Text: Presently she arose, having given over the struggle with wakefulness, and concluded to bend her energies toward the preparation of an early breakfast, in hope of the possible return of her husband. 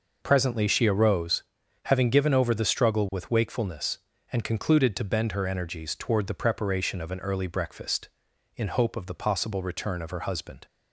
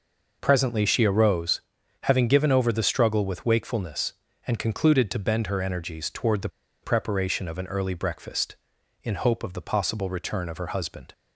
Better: first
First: none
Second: pauses between "the" and "preparation"; slight; at 6.4 s; 0.35 s long

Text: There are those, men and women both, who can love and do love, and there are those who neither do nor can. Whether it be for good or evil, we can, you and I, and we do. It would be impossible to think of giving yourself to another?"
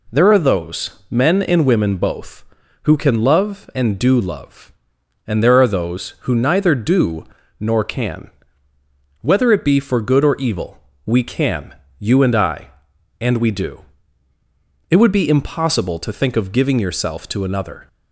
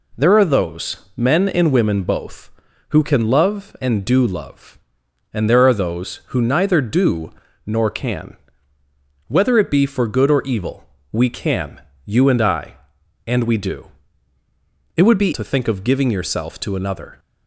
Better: first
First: pauses between "do" and "nor"; slight; at 7.2 s; 0.34 s long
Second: pauses between "do" and "nor"; slight; at 7.3 s; 0.34 s long // skips "impossible"; at 15.3 s

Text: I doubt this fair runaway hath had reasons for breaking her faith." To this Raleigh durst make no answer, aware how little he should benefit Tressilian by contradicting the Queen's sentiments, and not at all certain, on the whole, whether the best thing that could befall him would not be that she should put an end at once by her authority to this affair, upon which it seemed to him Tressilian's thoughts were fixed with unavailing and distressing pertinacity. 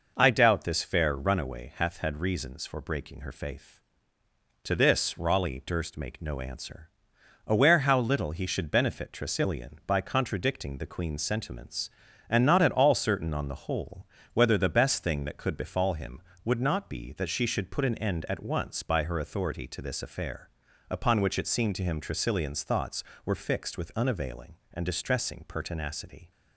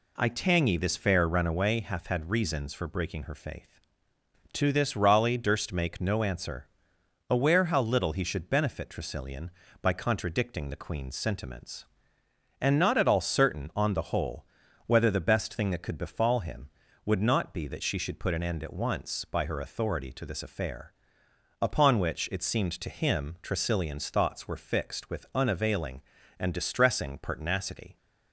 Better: first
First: none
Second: says "tangy" for "doubt"; at 0.2 s

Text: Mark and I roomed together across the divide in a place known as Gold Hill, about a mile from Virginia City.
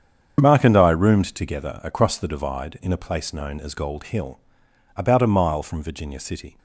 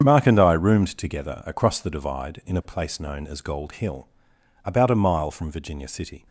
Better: neither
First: starts louder than the rest; strong; until 1.4 s; 7.5 dB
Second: starts louder than the rest; strong; until 1.0 s; 7.5 dB

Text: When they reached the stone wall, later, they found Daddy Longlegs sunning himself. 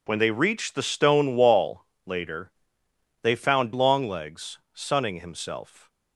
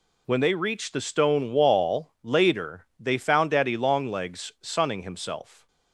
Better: second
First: skips "Daddy"; at 3.7 s // pauses between "Longlegs" and "sunning"; slight; at 4.5 s; 0.16 s long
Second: none

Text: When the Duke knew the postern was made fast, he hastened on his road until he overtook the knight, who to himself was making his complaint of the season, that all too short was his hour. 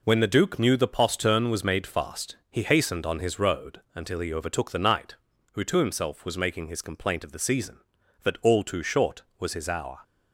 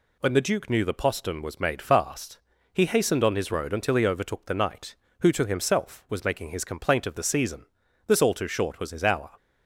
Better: first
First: none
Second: says "this" for "that"; at 8.0 s

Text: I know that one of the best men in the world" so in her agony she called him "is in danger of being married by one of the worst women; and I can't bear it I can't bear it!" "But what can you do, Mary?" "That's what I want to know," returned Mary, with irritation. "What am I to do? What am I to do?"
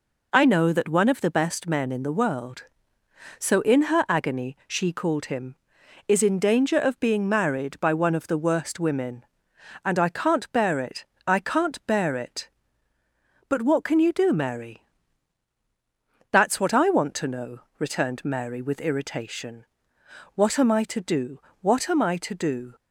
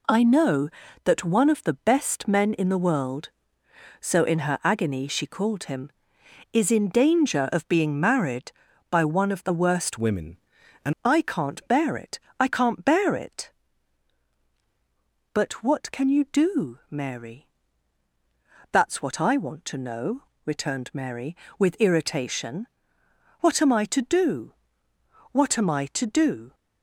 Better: first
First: pauses between "it" and "I"; slight; at 11.0 s; 0.20 s long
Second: changes voice from "women" to "and"; from 9.9 to 10.9 s; 1.0 s long // pauses between "it" and "I"; slight; at 12.1 s; 0.22 s long

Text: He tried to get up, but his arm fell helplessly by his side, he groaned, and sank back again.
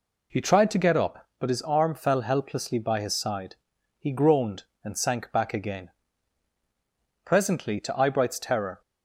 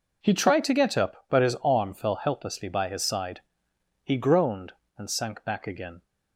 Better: second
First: goes on to say "Presently to Eyebright's terror"; from 7.2 s on; 1.5 s long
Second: none

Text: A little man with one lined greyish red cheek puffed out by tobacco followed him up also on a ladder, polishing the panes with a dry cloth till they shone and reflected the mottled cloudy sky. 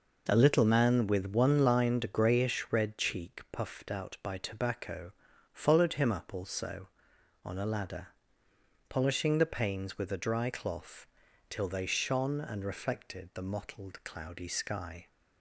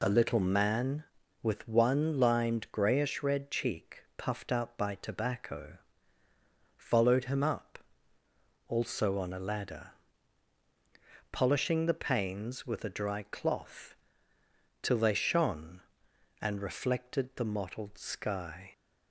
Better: first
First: pauses between "tobacco" and "followed"; at 5.1 s; 0.42 s long // pauses between "cloth" and "till"; at 11.0 s; 0.44 s long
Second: pauses between "tobacco" and "followed"; at 5.7 s; 1.0 s long // pauses between "up" and "also"; noticeable; at 7.7 s; 0.89 s long // pauses between "cloth" and "till"; noticeable; at 13.9 s; 0.88 s long // skips "cloudy"; at 17.9 s

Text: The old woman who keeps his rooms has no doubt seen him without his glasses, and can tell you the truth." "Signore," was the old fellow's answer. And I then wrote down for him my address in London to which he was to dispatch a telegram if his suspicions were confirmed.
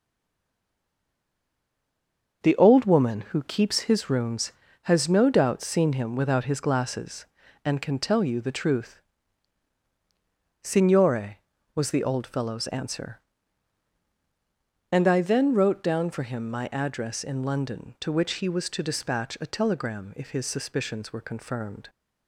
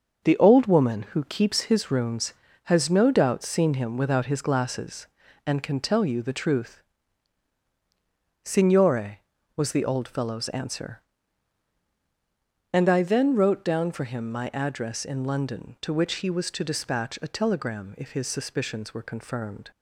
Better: second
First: stays silent before the first word; until 2.4 s; 2.4 s long // starts louder than the rest; until 3.5 s; 6.5 dB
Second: starts louder than the rest; until 1.3 s; 6.5 dB

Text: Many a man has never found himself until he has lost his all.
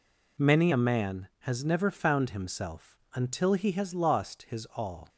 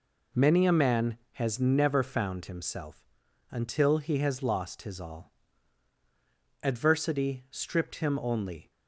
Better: first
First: pauses between "himself" and "until"; slight; at 2.9 s; 0.18 s long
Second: pauses between "himself" and "until"; at 3.0 s; 0.42 s long // goes on to say "Adversity stripped him only"; strong; from 6.6 s on; 2.0 s long

